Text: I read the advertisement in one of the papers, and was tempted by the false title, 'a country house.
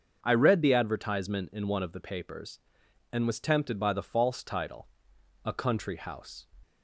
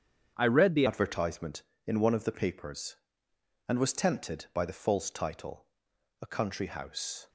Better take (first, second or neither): first